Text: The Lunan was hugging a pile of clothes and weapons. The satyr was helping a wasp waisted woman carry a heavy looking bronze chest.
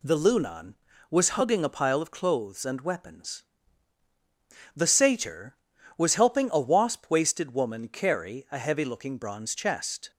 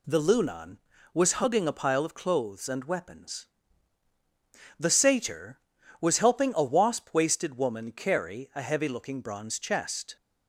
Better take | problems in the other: neither | none

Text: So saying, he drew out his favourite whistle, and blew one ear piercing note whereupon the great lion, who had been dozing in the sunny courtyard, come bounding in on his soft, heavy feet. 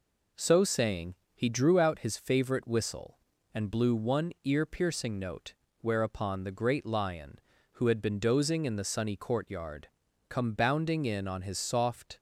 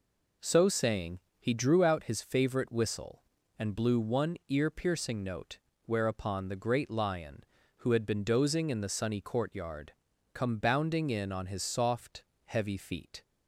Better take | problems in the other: second | pauses between "note" and "whereupon"; slight; at 5.5 s; 0.28 s long; slight in the second // stops before "heavy feet"; at 12.1 s

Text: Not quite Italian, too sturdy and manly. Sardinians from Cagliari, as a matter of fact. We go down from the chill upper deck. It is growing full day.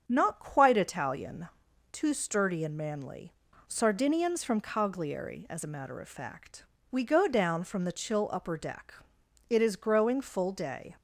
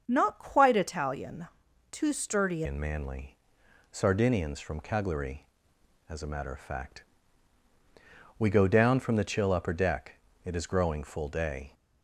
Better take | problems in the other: first | starts louder than the rest; until 1.0 s; 7 dB; also in the first // changes voice at "and"; from 2.6 s on; 9.1 s long

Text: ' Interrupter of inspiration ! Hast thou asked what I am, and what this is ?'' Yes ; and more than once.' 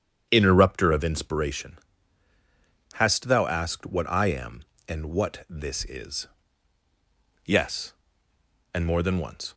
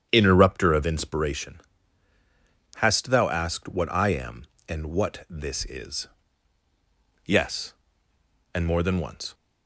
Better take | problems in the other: neither | starts louder than the rest; strong; the same in both

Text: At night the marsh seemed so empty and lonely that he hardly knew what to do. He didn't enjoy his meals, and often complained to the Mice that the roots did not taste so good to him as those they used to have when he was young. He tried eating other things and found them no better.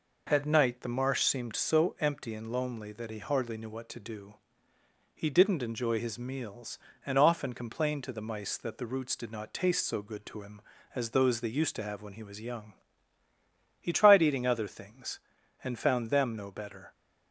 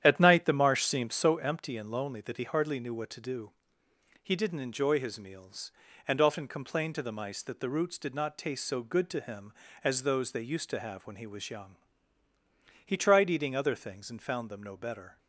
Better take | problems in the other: first | starts louder than the rest; strong; until 1.4 s; 10 dB

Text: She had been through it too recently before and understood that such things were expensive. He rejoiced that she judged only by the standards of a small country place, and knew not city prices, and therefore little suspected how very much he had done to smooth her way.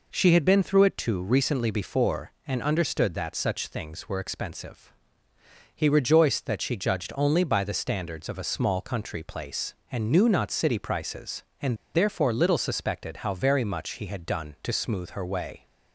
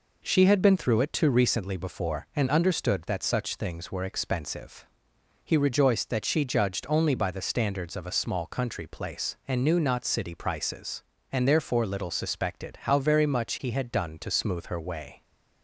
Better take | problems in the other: second | pauses between "and" and "therefore"; slight; at 11.7 s; 0.19 s long

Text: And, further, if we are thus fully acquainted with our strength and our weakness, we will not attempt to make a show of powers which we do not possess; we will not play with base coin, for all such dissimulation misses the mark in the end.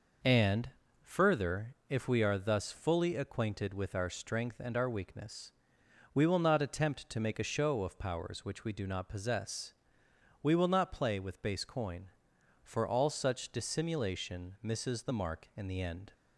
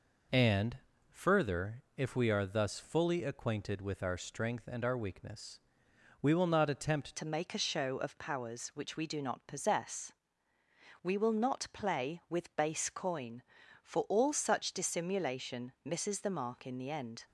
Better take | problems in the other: first | changes voice at "to"; from 7.1 s on; 10.1 s long

